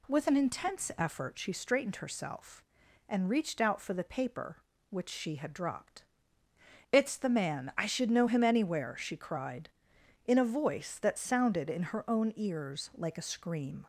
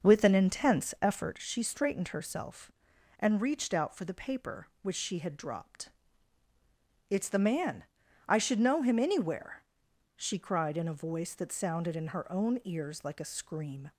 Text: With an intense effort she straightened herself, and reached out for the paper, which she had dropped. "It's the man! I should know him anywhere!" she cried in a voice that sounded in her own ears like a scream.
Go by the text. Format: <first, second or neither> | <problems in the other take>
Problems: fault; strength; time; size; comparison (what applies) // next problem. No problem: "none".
first | starts louder than the rest; until 1.4 s; 6.5 dB